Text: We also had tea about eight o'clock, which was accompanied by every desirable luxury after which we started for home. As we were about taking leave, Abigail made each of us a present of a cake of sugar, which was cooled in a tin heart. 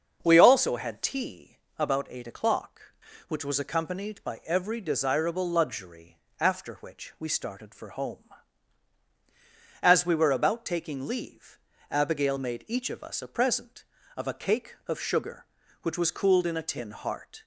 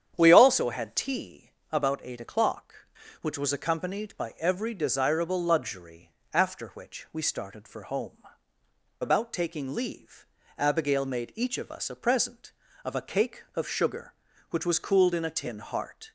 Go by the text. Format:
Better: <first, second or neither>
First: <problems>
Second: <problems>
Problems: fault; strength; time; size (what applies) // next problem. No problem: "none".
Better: first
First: starts louder than the rest; until 1.2 s; 6.5 dB // pauses between "tea" and "about"; slight; at 1.5 s; 0.22 s long // pauses between "luxury" and "after"; slight; at 6.1 s; 0.20 s long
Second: starts louder than the rest; strong; until 1.1 s; 9 dB // pauses between "tea" and "about"; slight; at 1.5 s; 0.22 s long // pauses between "luxury" and "after"; slight; at 6.1 s; 0.20 s long // skips "As we were"; at 8.5 s